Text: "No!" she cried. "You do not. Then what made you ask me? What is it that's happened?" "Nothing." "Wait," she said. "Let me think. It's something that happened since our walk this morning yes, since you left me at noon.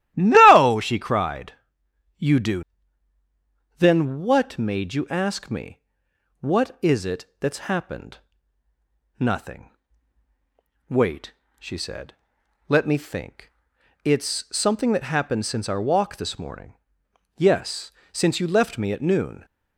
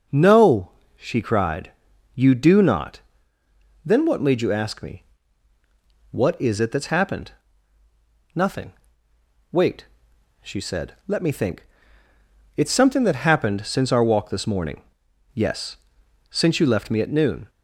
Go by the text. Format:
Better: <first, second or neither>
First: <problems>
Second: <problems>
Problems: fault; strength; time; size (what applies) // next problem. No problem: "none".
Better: second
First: starts louder than the rest; strong; until 1.1 s; 13.5 dB // skips "not"; at 3.2 s // pauses between "it" and "that's"; slight; at 7.2 s; 0.16 s long // pauses between "morning" and "yes"; noticeable; at 16.7 s; 0.62 s long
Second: pauses between "morning" and "yes"; noticeable; at 14.8 s; 0.52 s long